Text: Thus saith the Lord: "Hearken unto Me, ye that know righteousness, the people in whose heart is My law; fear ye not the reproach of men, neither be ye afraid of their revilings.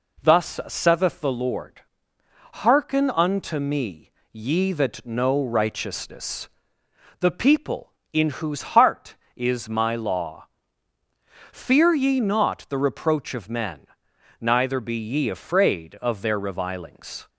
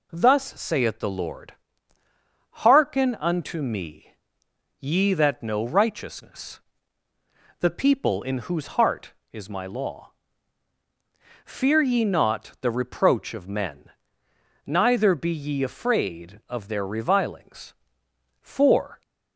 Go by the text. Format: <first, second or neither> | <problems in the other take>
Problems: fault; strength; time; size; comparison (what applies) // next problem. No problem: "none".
first | goes on to say "For"; noticeable; from 18.3 s on; 0.62 s long